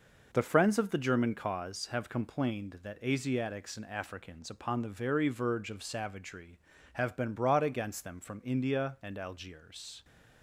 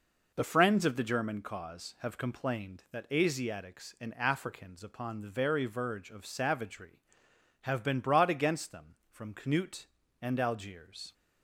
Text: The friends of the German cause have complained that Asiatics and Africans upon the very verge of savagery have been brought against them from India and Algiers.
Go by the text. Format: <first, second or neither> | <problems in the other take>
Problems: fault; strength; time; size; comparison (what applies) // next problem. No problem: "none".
first | says "Knut" for "India"; at 9.3 s